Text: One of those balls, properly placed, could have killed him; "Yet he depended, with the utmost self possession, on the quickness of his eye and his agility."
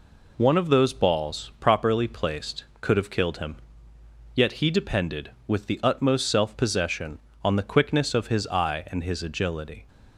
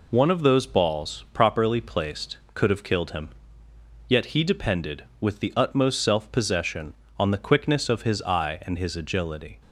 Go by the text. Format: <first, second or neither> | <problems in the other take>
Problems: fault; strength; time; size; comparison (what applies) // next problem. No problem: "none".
neither | none